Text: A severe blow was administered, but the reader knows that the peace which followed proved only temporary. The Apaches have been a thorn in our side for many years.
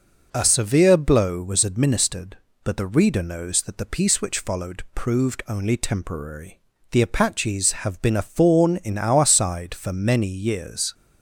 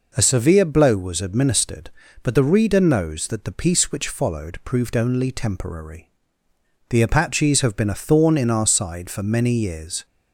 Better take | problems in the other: neither | none

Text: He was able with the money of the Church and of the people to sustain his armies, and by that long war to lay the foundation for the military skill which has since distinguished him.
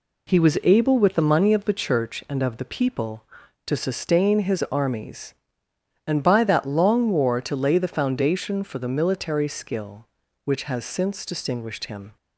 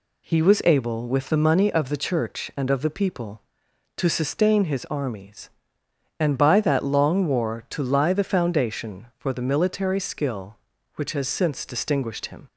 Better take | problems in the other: first | says "lie" for "lay"; at 7.8 s

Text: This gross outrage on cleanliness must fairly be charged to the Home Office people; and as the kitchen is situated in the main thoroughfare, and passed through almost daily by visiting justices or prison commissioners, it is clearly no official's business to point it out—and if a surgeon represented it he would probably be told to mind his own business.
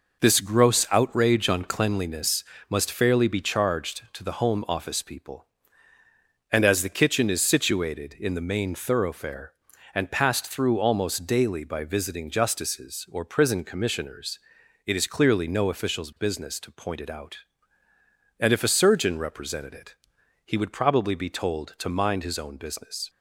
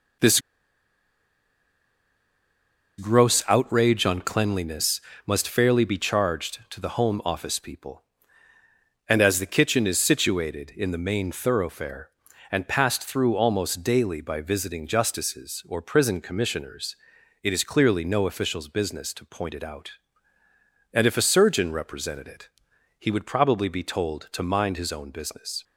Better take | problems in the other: first | pauses between "This" and "gross"; strong; at 0.4 s; 2.5 s long // pauses between "cleanliness" and "must"; slight; at 4.9 s; 0.26 s long; slight in the first // pauses between "it" and "he"; noticeable; at 22.4 s; 0.50 s long; noticeable in the first

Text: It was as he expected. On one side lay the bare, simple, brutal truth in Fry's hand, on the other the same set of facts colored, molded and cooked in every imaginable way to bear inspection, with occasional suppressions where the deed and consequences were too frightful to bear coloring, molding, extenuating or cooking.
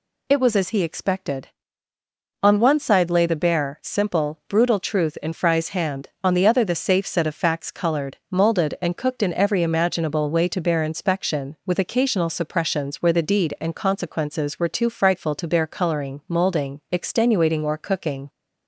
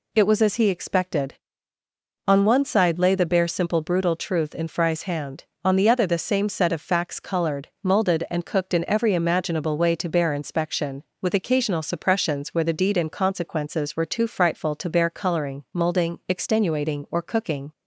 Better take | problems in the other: second | says "safe" for "same"; at 6.7 s

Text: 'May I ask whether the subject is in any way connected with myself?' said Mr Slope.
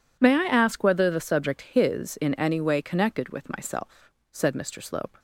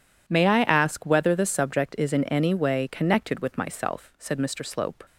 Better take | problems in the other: second | says "his" for "is"; at 1.6 s

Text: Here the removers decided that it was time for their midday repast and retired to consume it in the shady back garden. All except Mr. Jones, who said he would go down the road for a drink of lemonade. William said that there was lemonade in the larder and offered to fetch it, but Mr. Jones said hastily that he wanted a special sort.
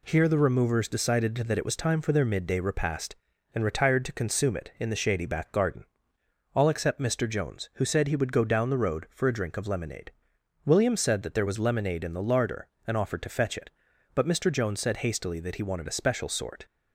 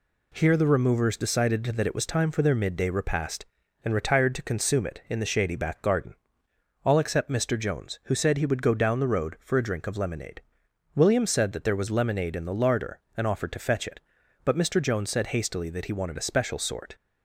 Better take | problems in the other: neither | none

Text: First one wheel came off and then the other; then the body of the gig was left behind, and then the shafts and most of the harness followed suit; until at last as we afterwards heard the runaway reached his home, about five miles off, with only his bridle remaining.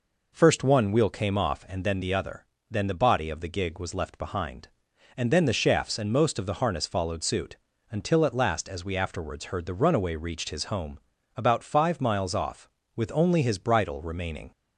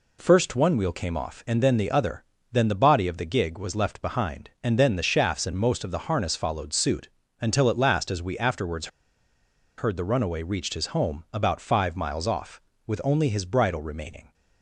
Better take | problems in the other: first | pauses between "afterwards" and "heard"; noticeable; at 8.8 s; 0.90 s long

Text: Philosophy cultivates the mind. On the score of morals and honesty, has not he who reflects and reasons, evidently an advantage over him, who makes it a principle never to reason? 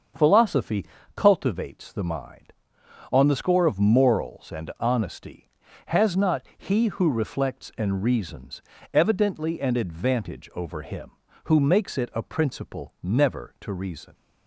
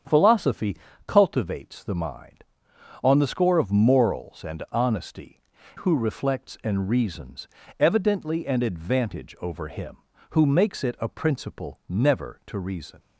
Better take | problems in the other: first | starts louder than the rest; strong; until 1.3 s; 8 dB; also in the first // pauses between "Philosophy" and "cultivates"; slight; at 0.7 s; 0.32 s long; slight in the first // skips "has not he"; at 5.5 s

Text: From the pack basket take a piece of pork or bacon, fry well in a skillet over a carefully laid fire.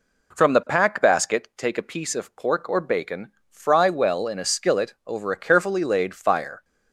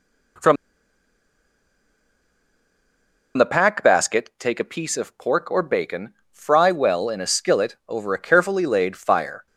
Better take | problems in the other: first | pauses between "From" and "the"; strong; at 0.5 s; 2.8 s long

